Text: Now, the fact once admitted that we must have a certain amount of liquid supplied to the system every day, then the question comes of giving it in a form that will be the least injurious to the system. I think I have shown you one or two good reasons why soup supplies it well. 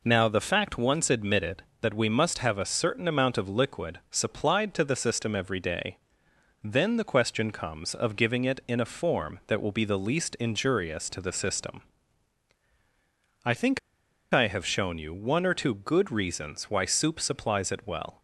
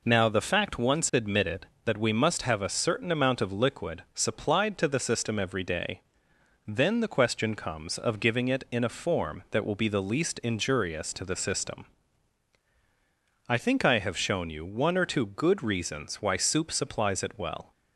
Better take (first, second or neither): second